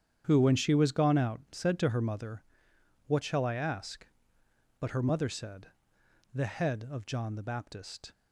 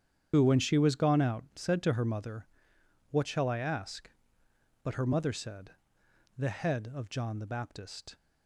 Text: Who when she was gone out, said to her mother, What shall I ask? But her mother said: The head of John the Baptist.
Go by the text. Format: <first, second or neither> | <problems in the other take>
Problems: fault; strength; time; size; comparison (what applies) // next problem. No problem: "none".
first | loses the start of "Who"; at 0.3 s; 55 ms // starts louder than the rest; strong; until 1.3 s; 8.5 dB; strong in the first